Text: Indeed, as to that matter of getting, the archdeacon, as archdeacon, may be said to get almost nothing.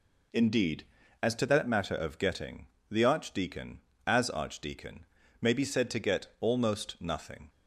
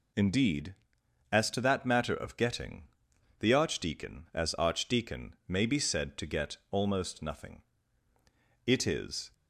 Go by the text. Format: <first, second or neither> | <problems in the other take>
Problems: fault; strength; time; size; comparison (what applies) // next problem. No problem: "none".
first | goes on to say "It is"; noticeable; from 8.6 s on; 0.64 s long